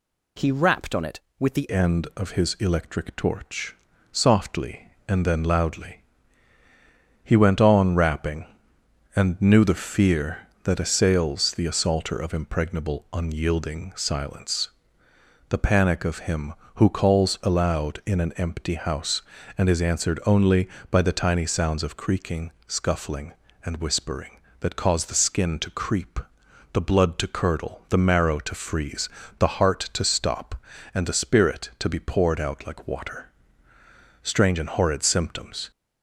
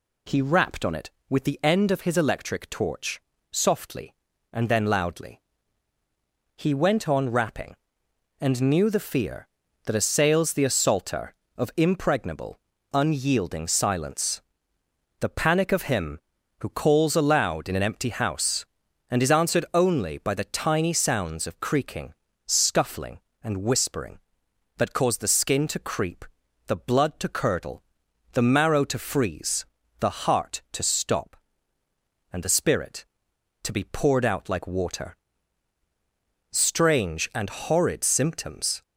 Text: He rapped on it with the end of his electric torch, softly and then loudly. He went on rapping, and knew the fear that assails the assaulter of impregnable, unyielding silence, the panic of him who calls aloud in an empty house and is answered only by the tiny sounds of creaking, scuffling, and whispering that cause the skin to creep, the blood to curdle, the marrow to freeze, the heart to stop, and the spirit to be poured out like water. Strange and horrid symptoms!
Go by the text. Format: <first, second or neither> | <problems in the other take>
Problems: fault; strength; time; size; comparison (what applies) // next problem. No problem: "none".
second | changes voice at "end"; from 1.7 s on; 34.0 s long